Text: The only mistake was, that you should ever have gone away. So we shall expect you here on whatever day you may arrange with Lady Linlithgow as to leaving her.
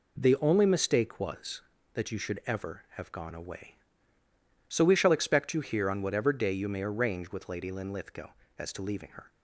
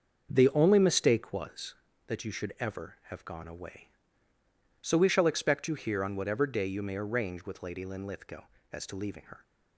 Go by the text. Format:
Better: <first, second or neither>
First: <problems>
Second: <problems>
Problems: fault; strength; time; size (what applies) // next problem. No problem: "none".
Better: first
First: none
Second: starts louder than the rest; until 1.4 s; 6.5 dB